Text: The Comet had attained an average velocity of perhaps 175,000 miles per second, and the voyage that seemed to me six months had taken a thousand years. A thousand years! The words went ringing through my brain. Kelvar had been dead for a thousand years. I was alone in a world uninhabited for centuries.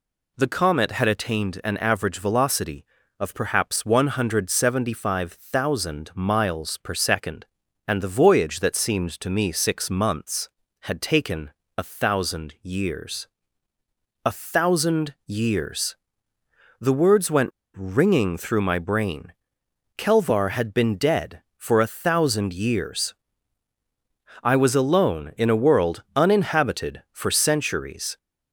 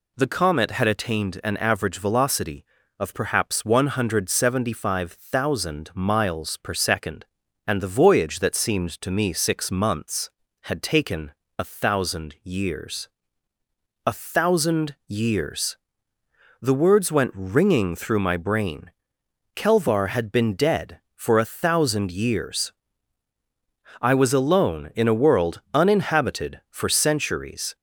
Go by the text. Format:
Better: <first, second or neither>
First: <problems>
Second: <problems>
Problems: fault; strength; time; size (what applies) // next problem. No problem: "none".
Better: second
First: pauses between "taken" and "a"; slight; at 11.5 s; 0.26 s long // pauses between "went" and "ringing"; slight; at 17.5 s; 0.23 s long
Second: pauses between "taken" and "a"; slight; at 11.3 s; 0.26 s long